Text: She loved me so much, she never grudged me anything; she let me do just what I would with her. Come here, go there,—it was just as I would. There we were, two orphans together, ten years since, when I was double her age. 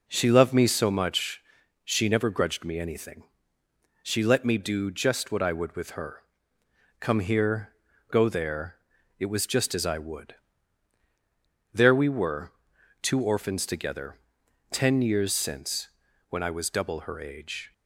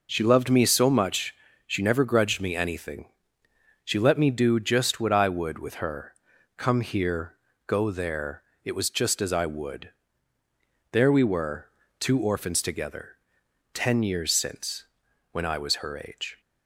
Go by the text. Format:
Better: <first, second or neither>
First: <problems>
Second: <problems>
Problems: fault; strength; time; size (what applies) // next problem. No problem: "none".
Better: first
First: none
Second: skips "double"; at 15.7 s